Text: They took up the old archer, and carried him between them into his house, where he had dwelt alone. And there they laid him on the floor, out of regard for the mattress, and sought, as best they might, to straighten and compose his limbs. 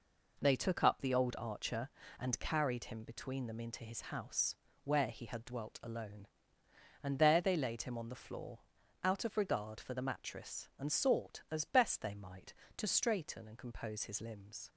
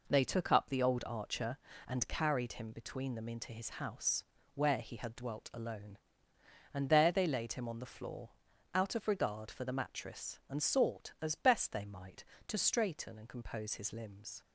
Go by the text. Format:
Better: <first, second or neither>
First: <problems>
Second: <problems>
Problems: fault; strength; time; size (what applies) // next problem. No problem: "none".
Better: neither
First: none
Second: none